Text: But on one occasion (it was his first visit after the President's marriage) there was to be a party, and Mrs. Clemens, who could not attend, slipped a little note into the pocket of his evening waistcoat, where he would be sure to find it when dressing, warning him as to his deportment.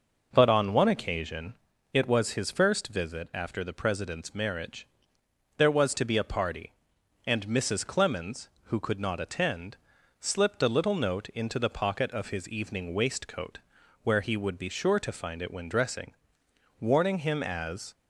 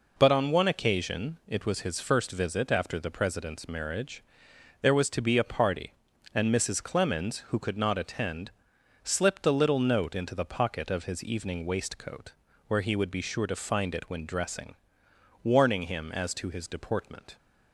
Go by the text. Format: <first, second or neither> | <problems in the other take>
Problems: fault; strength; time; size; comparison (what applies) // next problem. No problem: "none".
second | stops before "to his deportment"; at 17.9 s